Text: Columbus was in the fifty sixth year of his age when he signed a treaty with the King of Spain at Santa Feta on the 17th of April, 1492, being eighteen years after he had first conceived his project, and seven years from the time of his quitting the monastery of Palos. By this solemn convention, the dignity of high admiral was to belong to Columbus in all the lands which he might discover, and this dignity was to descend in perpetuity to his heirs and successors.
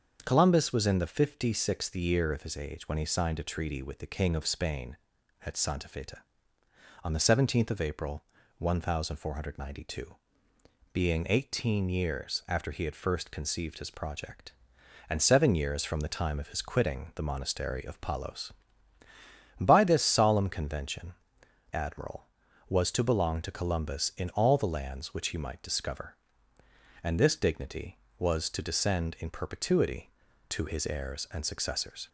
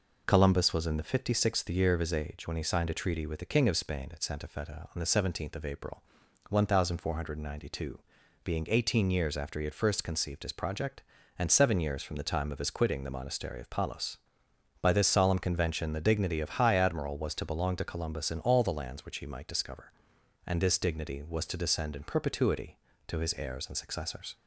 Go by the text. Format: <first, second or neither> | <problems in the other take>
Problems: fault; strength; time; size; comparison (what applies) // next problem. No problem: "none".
second | starts louder than the rest; until 1.2 s; 7 dB // skips "the dignity of high"; at 21.4 s